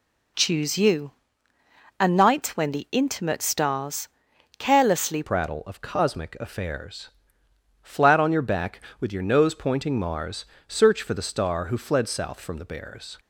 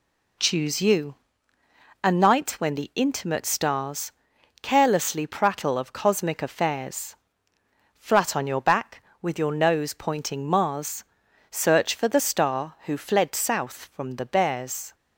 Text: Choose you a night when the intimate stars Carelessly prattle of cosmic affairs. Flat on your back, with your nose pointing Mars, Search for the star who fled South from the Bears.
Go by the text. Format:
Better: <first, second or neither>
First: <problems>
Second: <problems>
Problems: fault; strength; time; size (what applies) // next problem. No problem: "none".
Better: second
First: pauses between "you" and "a"; noticeable; at 1.1 s; 0.86 s long // pauses between "stars" and "Carelessly"; noticeable; at 4.0 s; 0.48 s long // changes voice at "prattle"; from 5.2 s on; 7.9 s long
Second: pauses between "you" and "a"; noticeable; at 1.1 s; 0.86 s long // pauses between "stars" and "Carelessly"; noticeable; at 4.1 s; 0.48 s long